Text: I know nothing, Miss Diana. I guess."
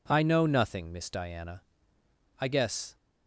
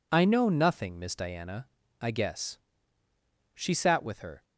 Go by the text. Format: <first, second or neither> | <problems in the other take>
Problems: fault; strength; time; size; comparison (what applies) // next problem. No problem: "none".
first | goes on to say "She sat with her"; noticeable; from 3.5 s on; 0.88 s long